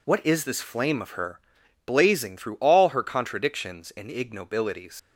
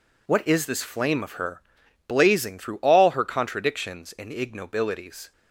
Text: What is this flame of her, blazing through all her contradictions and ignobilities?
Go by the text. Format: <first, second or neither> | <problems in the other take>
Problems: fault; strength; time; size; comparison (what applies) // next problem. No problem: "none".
second | leaves "ignobilities" unfinished; at 4.9 s; 105 ms